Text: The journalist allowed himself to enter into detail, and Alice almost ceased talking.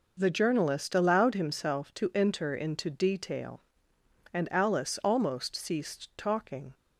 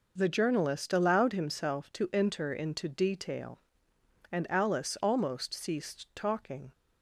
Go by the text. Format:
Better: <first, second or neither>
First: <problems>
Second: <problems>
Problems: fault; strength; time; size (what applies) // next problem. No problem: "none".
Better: neither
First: none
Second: none